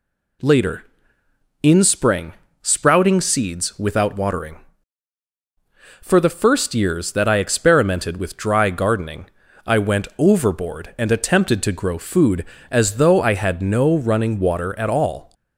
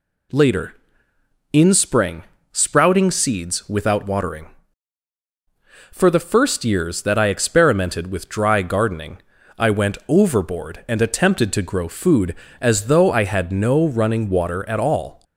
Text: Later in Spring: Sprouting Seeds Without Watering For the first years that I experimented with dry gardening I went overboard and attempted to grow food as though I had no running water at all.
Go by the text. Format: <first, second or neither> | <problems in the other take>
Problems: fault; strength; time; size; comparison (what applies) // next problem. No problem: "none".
neither | pauses between "gardening" and "I"; the same in both